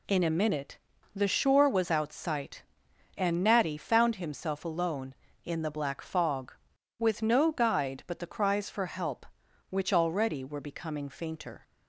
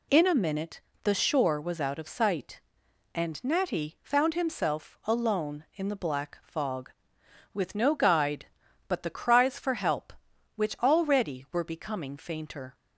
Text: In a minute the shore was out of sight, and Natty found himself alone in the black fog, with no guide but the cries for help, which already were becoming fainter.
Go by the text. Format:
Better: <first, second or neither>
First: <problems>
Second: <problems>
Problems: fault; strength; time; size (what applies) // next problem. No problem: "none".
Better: second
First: pauses between "minute" and "the"; at 0.7 s; 0.38 s long // skips "of"; at 2.1 s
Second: pauses between "minute" and "the"; slight; at 0.8 s; 0.24 s long